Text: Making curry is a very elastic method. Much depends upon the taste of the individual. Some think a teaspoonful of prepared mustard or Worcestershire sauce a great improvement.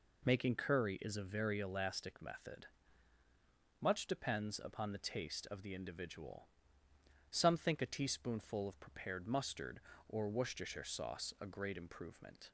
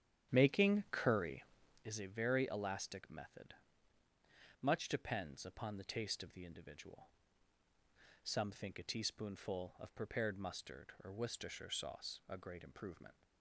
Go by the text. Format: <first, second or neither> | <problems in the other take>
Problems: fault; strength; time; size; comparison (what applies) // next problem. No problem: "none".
first | starts louder than the rest; strong; until 2.0 s; 10 dB